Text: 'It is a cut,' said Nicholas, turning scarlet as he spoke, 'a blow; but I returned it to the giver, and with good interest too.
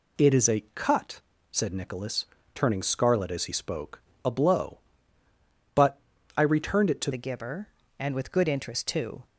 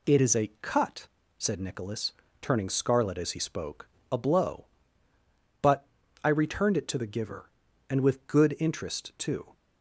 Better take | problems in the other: second | pauses between "but" and "I"; at 5.9 s; 0.38 s long; also in the second // changes voice at "the"; from 7.1 s on; 2.1 s long

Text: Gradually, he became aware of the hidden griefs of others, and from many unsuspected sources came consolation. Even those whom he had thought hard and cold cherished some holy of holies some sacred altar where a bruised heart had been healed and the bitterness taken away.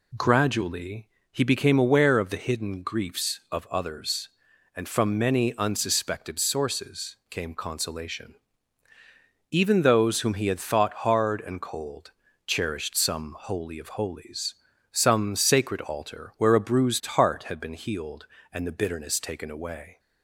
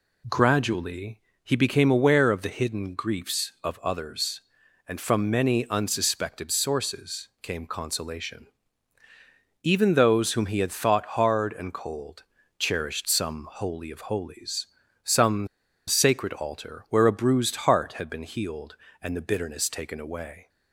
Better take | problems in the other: first | pauses between "cold" and "cherished"; slight; at 12.2 s; 0.34 s long; slight in the first // pauses between "holies" and "some"; at 14.6 s; 0.40 s long; also in the first // pauses between "some" and "sacred"; at 15.4 s; 0.40 s long

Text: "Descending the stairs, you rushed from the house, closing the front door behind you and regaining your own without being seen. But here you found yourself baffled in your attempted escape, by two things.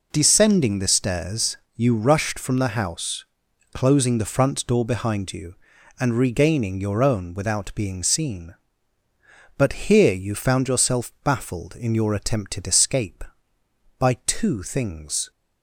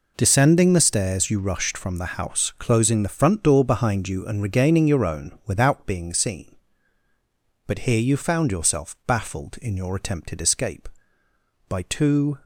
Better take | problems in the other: first | stops before "things"; at 12.4 s

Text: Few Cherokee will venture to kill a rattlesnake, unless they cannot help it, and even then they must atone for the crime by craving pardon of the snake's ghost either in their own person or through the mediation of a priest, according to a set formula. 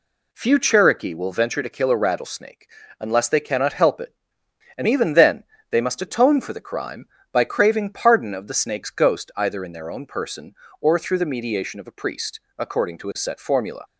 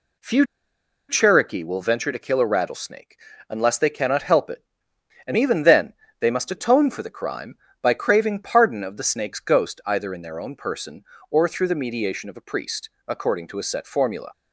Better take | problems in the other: first | pauses between "Few" and "Cherokee"; noticeable; at 0.4 s; 0.63 s long // pauses between "then" and "they"; slight; at 5.9 s; 0.26 s long; slight in the first

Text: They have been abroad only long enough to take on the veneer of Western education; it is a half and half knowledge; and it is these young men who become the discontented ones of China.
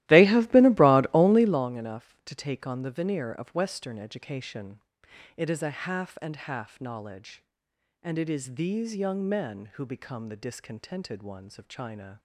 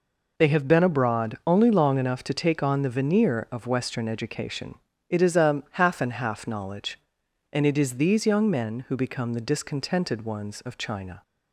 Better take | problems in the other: second | starts louder than the rest; strong; until 1.7 s; 15.5 dB

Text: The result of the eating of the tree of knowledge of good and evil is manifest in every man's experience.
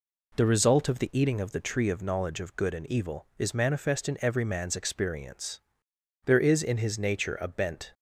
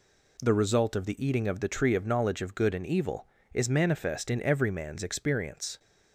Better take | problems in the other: second | goes on to say "There is in his nature a bent"; strong; from 6.2 s on; 1.6 s long

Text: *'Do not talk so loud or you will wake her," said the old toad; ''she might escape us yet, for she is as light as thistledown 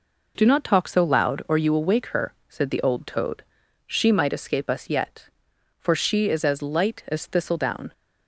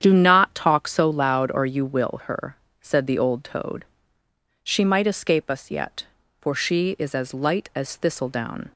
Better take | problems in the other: first | starts louder than the rest; strong; until 1.0 s; 9 dB // skips "wake"; at 2.2 s

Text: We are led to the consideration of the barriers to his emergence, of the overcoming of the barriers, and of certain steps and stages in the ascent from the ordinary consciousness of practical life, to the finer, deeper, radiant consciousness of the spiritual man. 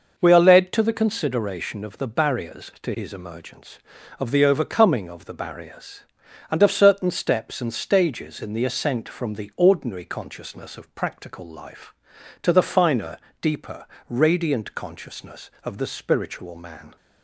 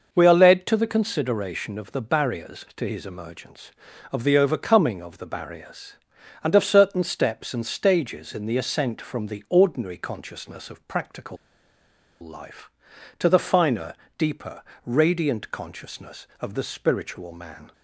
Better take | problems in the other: first | pauses between "practical" and "life"; noticeable; at 11.3 s; 0.85 s long

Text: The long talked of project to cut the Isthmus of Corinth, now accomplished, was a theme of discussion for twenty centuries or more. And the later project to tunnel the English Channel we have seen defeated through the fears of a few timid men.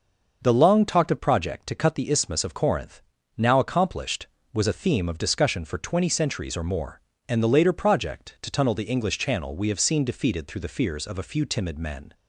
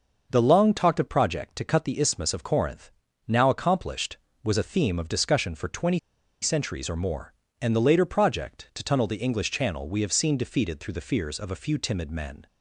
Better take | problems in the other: first | pauses between "twenty" and "centuries"; at 5.9 s; 0.43 s long

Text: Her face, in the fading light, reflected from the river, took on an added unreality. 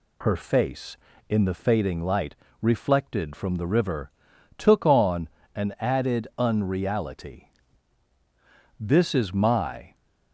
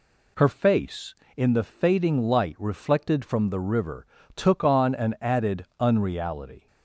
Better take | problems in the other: second | pauses between "on" and "an"; slight; at 5.2 s; 0.28 s long // goes on to say "This is my"; noticeable; from 8.7 s on; 1.1 s long

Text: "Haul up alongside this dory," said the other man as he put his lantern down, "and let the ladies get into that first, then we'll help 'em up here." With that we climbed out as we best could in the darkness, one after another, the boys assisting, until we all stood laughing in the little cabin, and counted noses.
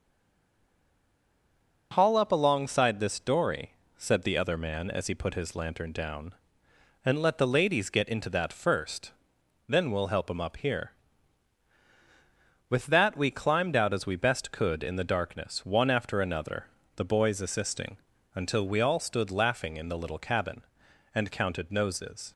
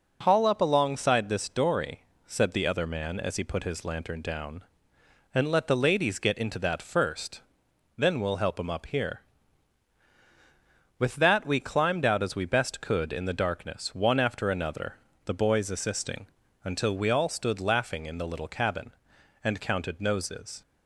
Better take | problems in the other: second | stays silent before the first word; noticeable; until 1.9 s; 1.9 s long

